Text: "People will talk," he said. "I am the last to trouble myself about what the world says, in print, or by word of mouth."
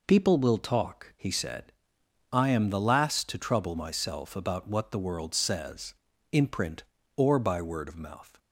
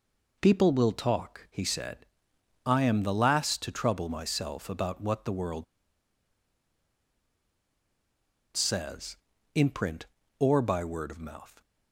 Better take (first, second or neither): first